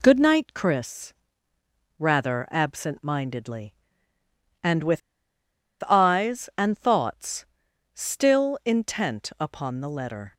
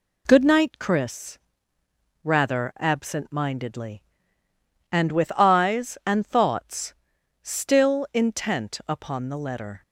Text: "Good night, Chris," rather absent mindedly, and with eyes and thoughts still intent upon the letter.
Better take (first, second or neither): second